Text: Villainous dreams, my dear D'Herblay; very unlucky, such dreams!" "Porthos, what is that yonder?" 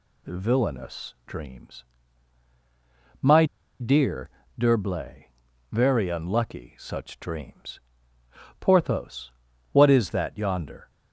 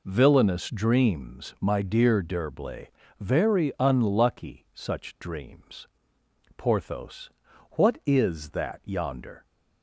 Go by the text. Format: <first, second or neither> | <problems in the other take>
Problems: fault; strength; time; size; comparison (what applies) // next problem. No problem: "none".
second | pauses between "my" and "dear"; slight; at 3.4 s; 0.34 s long // pauses between "dear" and "D'Herblay"; slight; at 4.2 s; 0.30 s long